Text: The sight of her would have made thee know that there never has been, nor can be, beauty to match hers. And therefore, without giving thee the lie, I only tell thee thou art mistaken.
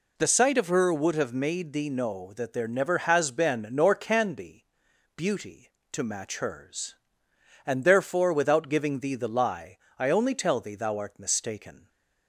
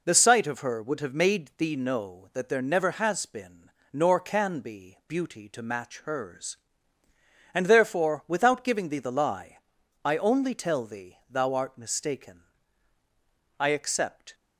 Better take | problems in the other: first | goes on to say "I accept"; noticeable; from 13.5 s on; 0.76 s long

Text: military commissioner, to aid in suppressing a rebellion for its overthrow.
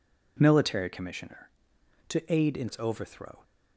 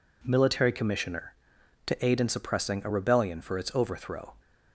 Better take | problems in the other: second | skips "suppressing a rebellion for"; at 2.6 s

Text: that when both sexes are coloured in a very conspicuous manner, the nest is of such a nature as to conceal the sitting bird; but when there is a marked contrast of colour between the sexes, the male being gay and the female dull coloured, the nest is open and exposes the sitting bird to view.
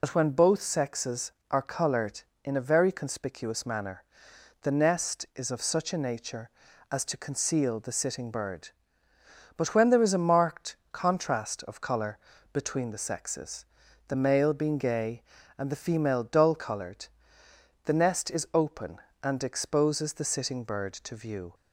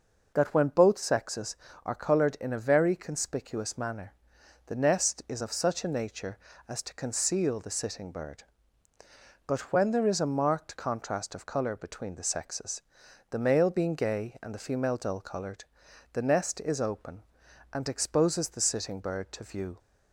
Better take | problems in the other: second | loses the start of "that"; at 0.0 s; 70 ms // pauses between "marked" and "contrast"; slight; at 10.7 s; 0.16 s long // pauses between "colour" and "between"; slight; at 12.1 s; 0.34 s long

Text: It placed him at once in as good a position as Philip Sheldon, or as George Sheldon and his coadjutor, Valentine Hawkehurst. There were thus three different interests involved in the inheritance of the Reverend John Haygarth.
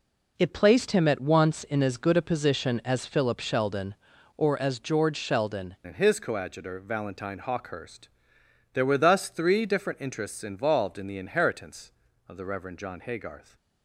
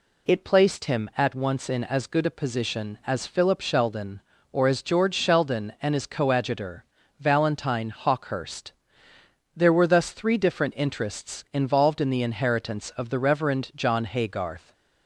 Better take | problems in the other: second | changes voice at "and"; from 5.8 s on; 7.7 s long

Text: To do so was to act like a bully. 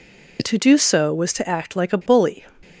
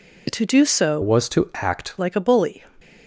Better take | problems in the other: first | changes voice from "was" to "act"; from 1.0 to 1.9 s; 0.9 s long

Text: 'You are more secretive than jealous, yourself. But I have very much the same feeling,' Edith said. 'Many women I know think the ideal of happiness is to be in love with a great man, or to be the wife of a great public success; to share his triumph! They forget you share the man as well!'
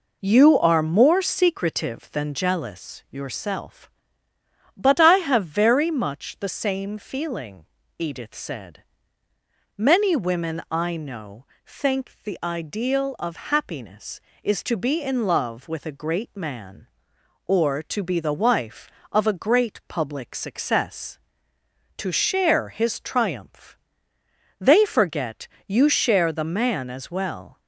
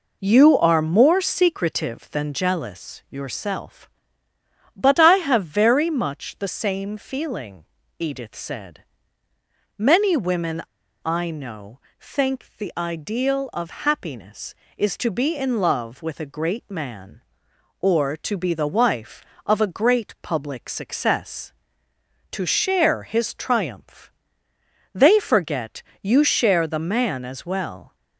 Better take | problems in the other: first | pauses between "women" and "I"; at 10.6 s; 0.45 s long // pauses between "know" and "think"; slight; at 11.7 s; 0.20 s long; slight in the first // pauses between "forget" and "you"; slight; at 25.8 s; 0.22 s long; slight in the first

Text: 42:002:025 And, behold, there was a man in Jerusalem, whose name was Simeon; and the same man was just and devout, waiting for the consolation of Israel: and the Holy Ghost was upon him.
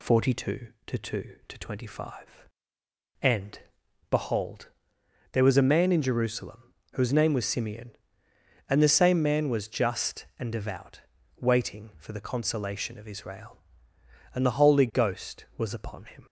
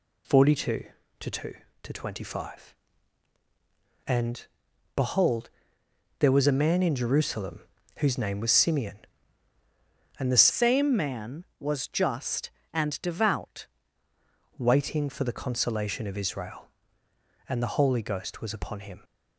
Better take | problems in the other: first | changes voice from "same" to "devout"; from 10.4 to 13.6 s; 3.2 s long

